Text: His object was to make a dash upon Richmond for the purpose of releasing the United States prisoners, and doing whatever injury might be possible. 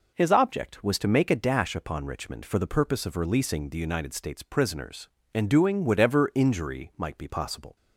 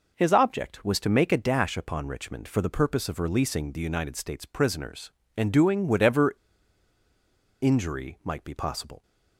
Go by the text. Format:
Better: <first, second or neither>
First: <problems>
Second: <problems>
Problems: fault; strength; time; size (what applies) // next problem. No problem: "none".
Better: first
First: none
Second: pauses between "whatever" and "injury"; strong; at 6.3 s; 1.2 s long